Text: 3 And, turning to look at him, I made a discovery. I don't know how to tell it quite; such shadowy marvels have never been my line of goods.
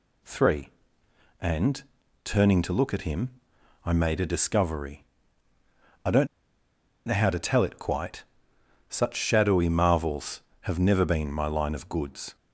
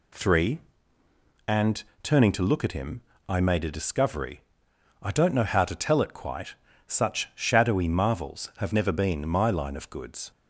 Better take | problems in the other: second | pauses between "don't" and "know"; noticeable; at 6.2 s; 0.80 s long

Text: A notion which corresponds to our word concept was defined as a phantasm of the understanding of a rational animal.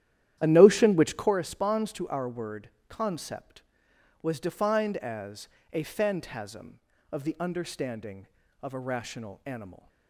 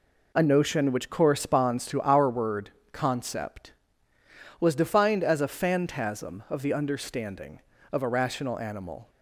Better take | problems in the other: second | starts louder than the rest; strong; until 1.3 s; 11.5 dB // pauses between "word" and "concept"; slight; at 2.6 s; 0.18 s long; slight in the second // pauses between "as" and "a"; slight; at 5.4 s; 0.24 s long

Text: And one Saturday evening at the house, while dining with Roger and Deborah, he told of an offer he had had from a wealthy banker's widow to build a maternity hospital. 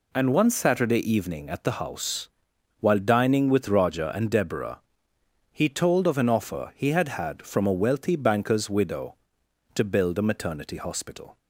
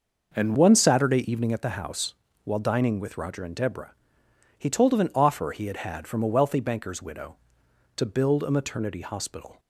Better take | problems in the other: first | changes voice at "one"; from 0.5 s on; 9.0 s long

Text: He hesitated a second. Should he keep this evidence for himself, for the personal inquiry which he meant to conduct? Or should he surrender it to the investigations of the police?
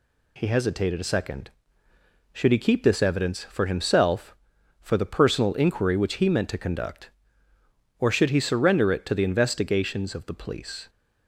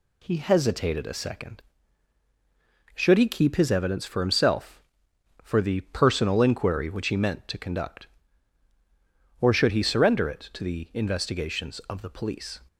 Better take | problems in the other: first | says "his" for "this"; at 3.5 s

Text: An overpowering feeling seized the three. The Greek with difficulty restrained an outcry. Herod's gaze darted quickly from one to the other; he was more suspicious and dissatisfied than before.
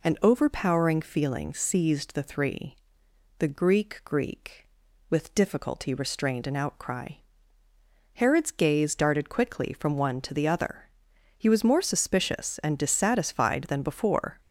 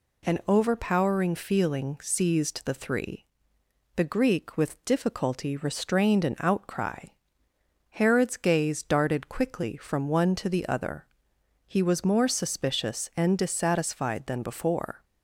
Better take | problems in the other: second | says "Greek" twice; at 4.0 s

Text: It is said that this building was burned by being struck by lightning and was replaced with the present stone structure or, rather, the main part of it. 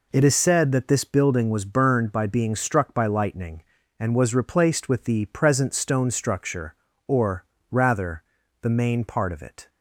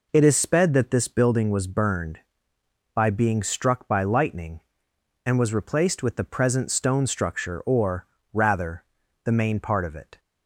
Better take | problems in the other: first | says "sped" for "said"; at 0.3 s

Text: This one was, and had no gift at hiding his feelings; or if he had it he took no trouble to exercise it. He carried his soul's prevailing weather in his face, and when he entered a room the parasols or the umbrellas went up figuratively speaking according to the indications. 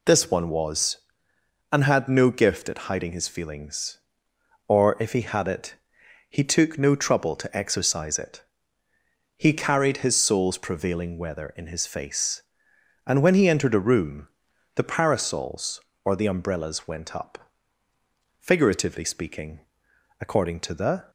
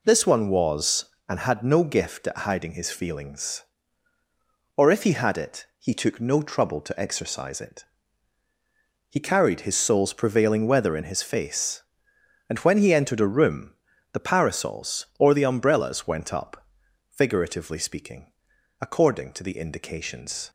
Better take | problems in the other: second | pauses between "it" and "he"; noticeable; at 5.7 s; 0.58 s long // pauses between "room" and "the"; noticeable; at 14.2 s; 0.48 s long; also in the second // pauses between "up" and "figuratively"; at 17.3 s; 1.0 s long; noticeable in the second // pauses between "speaking" and "according"; noticeable; at 19.5 s; 0.60 s long; noticeable in the second // stops before "indications"; at 21.0 s

